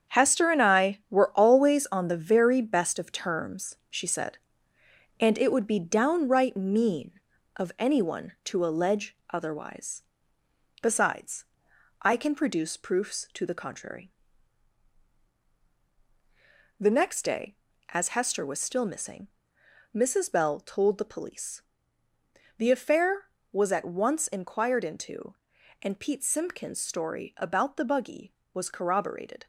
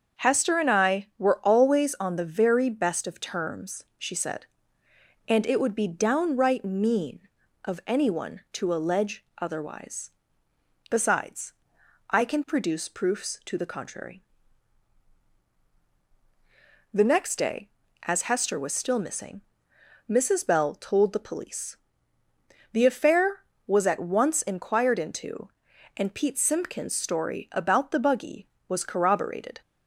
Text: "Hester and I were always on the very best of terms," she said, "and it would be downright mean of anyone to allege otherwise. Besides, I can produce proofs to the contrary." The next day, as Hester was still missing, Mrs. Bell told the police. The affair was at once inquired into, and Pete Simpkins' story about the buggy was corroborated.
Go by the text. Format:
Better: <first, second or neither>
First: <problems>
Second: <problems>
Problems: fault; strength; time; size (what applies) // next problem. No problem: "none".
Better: second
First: gets quieter; strong; throughout; 8.5 dB // starts louder than the rest; strong; until 1.2 s; 8 dB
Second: starts louder than the rest; until 1.3 s; 7 dB